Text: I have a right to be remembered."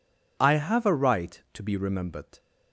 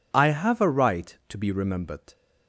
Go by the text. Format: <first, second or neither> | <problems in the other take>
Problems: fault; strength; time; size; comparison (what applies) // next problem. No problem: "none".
neither | none